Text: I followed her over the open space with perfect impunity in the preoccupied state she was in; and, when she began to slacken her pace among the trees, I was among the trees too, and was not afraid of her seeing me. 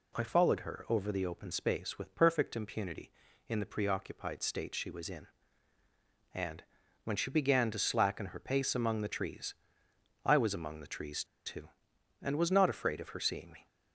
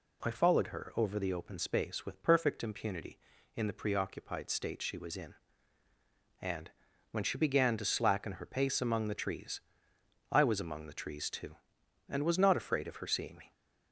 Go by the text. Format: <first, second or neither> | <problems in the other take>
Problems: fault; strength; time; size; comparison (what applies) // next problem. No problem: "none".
second | pauses between "trees" and "too"; slight; at 11.2 s; 0.21 s long